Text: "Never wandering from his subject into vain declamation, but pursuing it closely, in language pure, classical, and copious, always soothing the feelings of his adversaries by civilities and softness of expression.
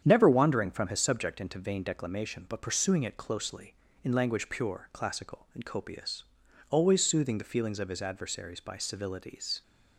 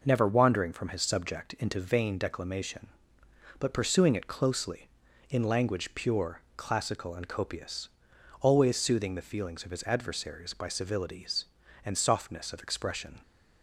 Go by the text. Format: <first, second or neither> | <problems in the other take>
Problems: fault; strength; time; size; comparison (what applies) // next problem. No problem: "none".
second | starts louder than the rest; strong; until 1.0 s; 8.5 dB // stops before "and softness of expression"; at 9.6 s